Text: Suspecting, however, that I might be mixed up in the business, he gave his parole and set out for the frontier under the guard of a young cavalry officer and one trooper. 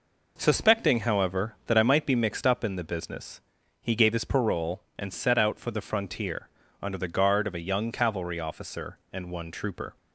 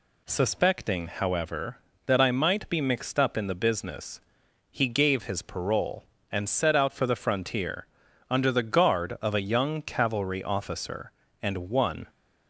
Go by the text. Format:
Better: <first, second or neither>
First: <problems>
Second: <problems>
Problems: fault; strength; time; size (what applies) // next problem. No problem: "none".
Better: first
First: pauses between "frontier" and "under"; slight; at 6.4 s; 0.32 s long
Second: pauses between "frontier" and "under"; at 7.8 s; 0.44 s long // stops before "trooper"; at 12.0 s